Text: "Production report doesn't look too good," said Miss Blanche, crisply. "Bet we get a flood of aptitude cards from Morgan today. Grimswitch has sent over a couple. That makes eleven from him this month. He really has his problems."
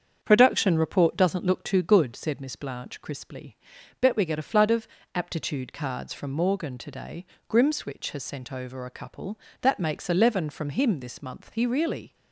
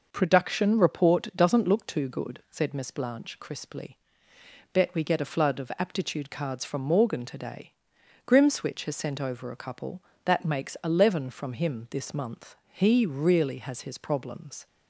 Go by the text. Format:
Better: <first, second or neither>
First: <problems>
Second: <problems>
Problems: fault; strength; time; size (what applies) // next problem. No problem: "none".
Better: second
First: starts louder than the rest; strong; until 1.2 s; 7.5 dB // pauses between "of" and "aptitude"; slight; at 4.8 s; 0.30 s long // stops before "has his problems"; at 12.1 s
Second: none